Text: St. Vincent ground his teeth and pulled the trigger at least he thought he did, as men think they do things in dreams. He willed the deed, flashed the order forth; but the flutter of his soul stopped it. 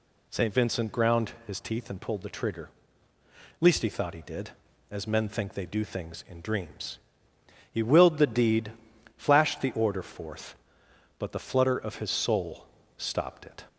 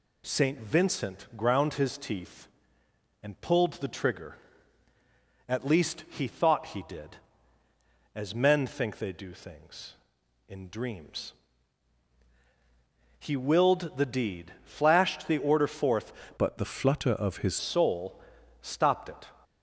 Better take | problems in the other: first | changes voice from "but" to "his"; from 16.3 to 17.5 s; 1.2 s long // pauses between "soul" and "stopped"; at 18.1 s; 0.44 s long; slight in the first

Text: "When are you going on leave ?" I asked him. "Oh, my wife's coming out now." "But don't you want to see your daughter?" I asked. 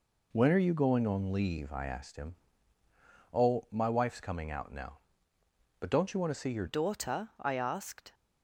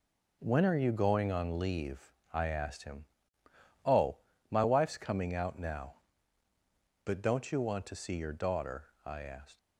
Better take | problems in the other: second | changes voice at "daughter"; from 6.6 s on; 1.5 s long

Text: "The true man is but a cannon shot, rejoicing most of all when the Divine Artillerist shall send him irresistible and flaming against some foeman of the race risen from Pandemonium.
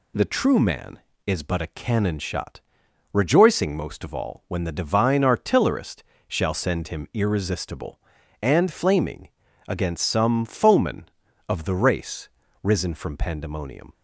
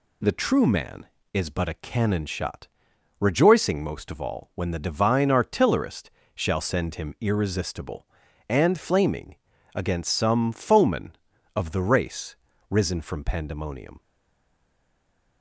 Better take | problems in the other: first | pauses between "Artillerist" and "shall"; slight; at 6.1 s; 0.24 s long; slight in the first // pauses between "flaming" and "against"; at 9.3 s; 0.40 s long; also in the first // pauses between "race" and "risen"; slight; at 12.3 s; 0.34 s long; slight in the first // stays silent after the last word; noticeable; from 13.9 s on; 1.5 s long

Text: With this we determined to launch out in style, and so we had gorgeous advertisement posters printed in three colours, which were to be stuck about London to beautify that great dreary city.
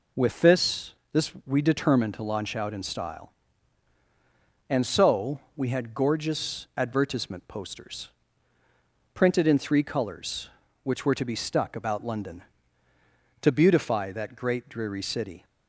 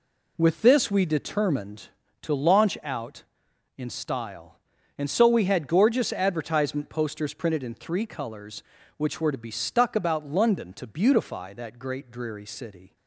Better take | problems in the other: second | says "this" twice; at 1.1 s // pauses between "so" and "we"; slight; at 5.4 s; 0.16 s long // pauses between "posters" and "printed"; at 8.0 s; 1.0 s long

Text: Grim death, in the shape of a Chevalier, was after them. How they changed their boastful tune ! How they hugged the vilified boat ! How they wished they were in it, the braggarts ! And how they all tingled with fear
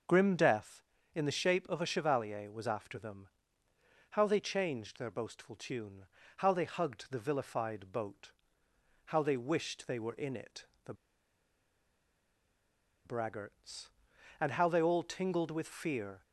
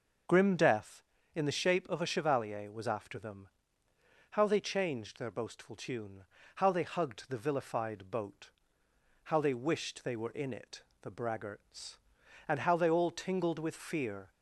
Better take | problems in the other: second | starts louder than the rest; noticeable; until 1.4 s; 6 dB; noticeable in the second // pauses between "the" and "braggarts"; strong; at 10.9 s; 2.1 s long

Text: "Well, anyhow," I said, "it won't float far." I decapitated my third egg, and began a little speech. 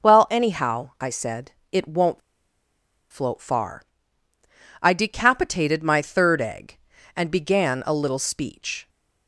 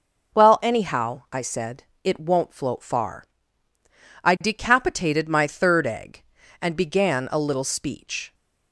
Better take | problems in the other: second | pauses between "won't" and "float"; noticeable; at 2.2 s; 0.92 s long

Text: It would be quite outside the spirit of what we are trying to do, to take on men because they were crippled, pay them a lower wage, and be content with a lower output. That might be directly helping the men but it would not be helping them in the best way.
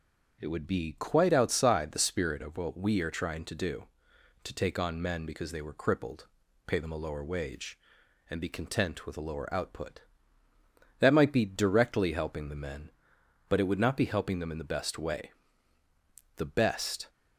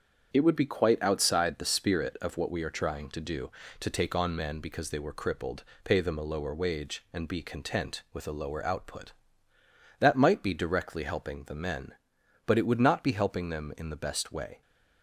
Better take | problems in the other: second | starts louder than the rest; strong; until 1.4 s; 7.5 dB; strong in the second // goes on to say "The best"; noticeable; from 16.3 s on; 0.72 s long

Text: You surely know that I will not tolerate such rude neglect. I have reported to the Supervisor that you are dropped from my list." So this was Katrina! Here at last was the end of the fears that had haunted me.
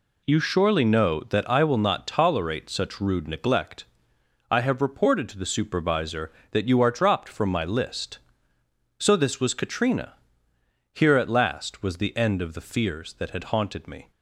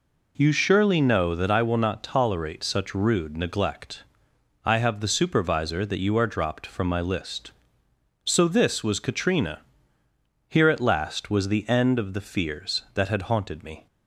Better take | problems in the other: first | skips "reported to"; at 5.0 s

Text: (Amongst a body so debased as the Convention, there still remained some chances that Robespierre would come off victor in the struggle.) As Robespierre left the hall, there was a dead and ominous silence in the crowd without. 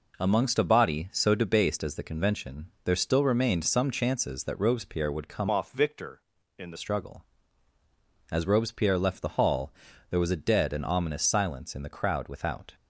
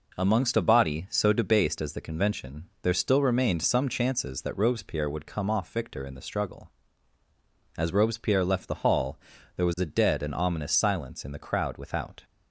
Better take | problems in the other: second | changes voice from "off" to "the"; from 5.5 to 6.7 s; 1.2 s long

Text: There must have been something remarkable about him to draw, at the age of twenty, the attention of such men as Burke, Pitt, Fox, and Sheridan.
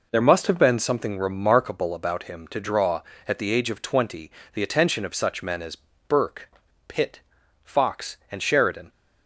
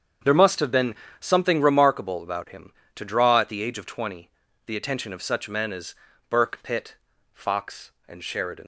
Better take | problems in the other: first | starts louder than the rest; strong; until 1.5 s; 7.5 dB // pauses between "been" and "something"; slight; at 0.9 s; 0.26 s long // pauses between "as" and "Burke"; slight; at 5.9 s; 0.34 s long; slight in the first // leaves "Sheridan" unfinished; at 8.6 s; 85 ms

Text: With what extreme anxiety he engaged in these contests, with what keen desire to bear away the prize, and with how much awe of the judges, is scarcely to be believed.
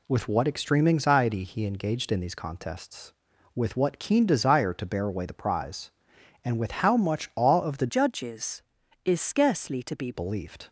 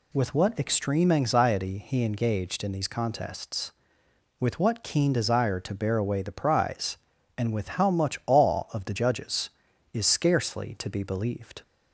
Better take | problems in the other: second | changes voice from "judges" to "be"; from 7.8 to 10.1 s; 2.3 s long

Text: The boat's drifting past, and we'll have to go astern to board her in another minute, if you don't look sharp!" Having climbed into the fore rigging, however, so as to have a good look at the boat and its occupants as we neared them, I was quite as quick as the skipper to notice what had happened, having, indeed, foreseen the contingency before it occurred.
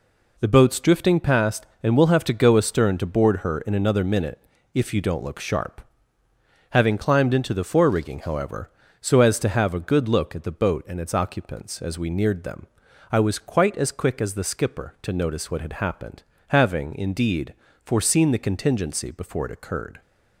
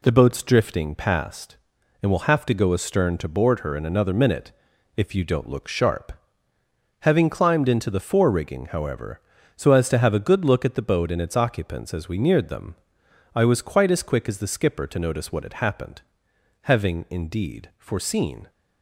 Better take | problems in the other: first | stops before "the contingency before it occurred"; at 18.4 s

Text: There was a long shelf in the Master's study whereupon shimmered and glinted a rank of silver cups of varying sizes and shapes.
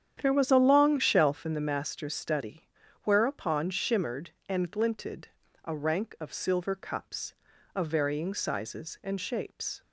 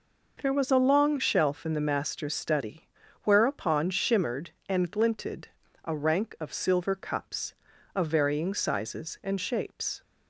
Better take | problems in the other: second | starts louder than the rest; strong; until 1.6 s; 9 dB // pauses between "study" and "whereupon"; at 2.6 s; 0.38 s long; also in the second // pauses between "glinted" and "a"; slight; at 5.2 s; 0.34 s long; slight in the second

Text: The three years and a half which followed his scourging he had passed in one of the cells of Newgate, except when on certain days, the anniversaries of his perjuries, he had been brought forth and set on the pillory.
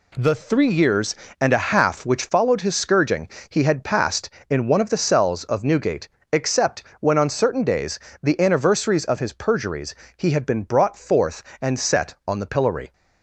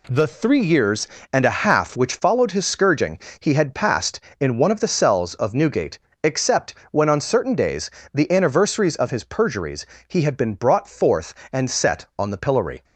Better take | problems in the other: neither | pauses between "scourging" and "he"; slight; the same in both // pauses between "except" and "when"; slight; the same in both

